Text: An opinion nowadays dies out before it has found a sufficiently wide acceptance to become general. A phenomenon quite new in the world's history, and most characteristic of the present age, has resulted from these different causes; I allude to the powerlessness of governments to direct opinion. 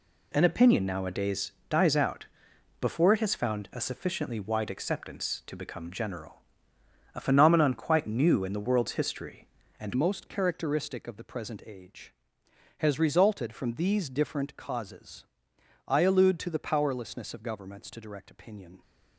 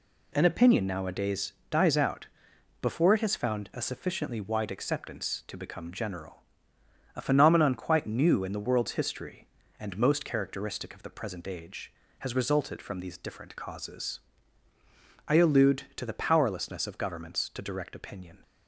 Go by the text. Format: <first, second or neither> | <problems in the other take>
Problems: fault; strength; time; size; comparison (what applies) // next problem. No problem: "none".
second | pauses between "nowadays" and "dies"; slight; at 1.5 s; 0.18 s long; slight in the second // pauses between "out" and "before"; noticeable; at 2.2 s; 0.56 s long; noticeable in the second // changes voice at "most"; from 9.9 s on; 8.9 s long